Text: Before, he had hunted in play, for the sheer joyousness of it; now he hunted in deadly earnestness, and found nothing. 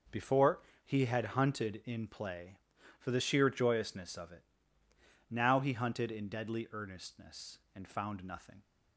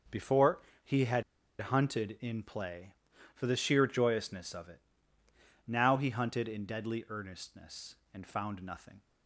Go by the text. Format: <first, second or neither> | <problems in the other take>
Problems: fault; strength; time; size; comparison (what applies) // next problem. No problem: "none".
first | pauses between "had" and "hunted"; at 1.2 s; 0.37 s long